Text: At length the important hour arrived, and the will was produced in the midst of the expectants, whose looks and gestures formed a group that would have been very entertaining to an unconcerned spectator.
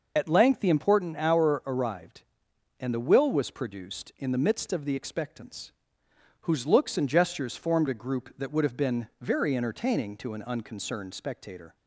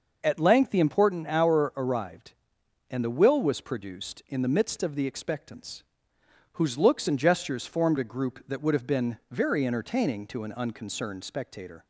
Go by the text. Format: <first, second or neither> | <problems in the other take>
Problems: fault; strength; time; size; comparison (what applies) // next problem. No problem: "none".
second | loses the start of "At"; at 0.1 s; 40 ms